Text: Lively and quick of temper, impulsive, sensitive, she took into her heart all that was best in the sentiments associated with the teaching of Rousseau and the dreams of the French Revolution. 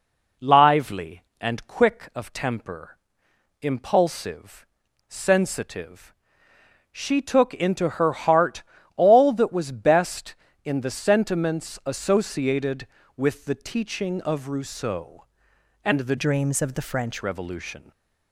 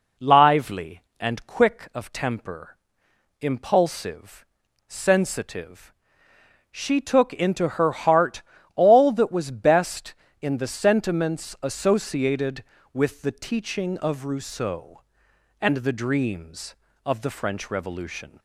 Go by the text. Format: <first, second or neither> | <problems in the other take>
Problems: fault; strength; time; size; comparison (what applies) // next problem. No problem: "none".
second | pauses between "heart" and "all"; slight; at 8.6 s; 0.34 s long; slight in the second // changes voice from "dreams" to "French"; from 16.1 to 17.2 s; 1.1 s long